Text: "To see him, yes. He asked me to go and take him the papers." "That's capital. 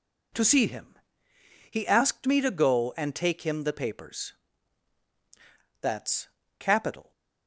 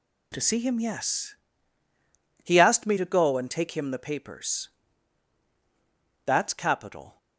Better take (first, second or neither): second